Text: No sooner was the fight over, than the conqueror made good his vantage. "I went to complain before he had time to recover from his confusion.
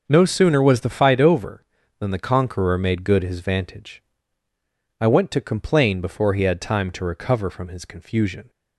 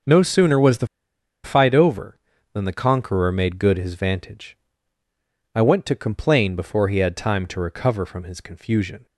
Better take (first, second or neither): first